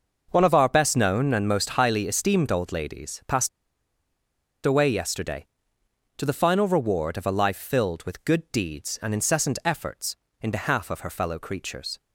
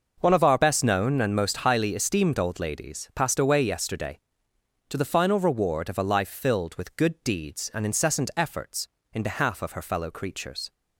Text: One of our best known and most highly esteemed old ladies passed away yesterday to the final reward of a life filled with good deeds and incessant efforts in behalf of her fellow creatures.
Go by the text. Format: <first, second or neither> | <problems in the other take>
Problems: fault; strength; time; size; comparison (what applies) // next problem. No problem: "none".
second | pauses between "passed" and "away"; at 3.4 s; 1.1 s long